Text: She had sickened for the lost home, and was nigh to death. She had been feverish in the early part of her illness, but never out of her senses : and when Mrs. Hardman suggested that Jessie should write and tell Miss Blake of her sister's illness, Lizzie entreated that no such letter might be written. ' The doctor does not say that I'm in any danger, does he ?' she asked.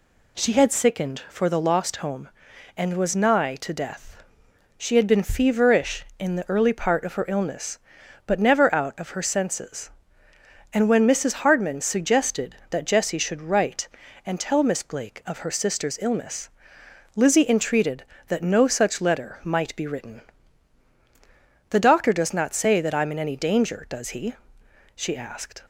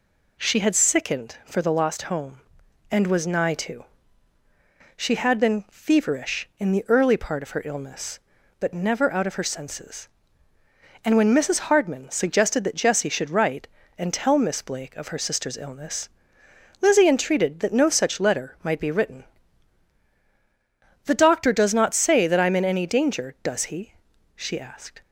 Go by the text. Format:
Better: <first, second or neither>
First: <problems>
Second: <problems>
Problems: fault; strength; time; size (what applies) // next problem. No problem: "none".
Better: first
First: none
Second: skips "death"; at 4.4 s